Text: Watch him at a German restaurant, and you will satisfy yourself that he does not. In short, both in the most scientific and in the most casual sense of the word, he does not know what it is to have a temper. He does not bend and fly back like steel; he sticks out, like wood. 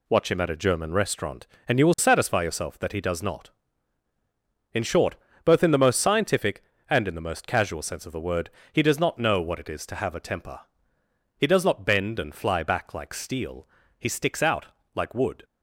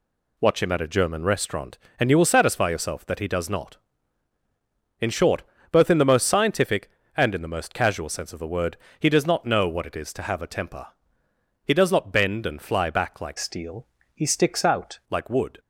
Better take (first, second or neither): first